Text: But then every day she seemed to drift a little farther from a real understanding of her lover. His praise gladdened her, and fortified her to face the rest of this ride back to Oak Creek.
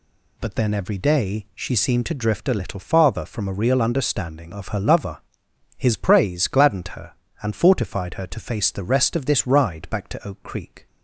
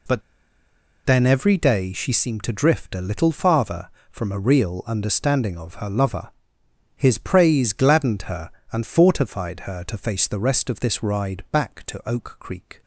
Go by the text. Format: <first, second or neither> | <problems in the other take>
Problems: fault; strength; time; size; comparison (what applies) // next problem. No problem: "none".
first | pauses between "But" and "then"; noticeable; at 0.2 s; 0.84 s long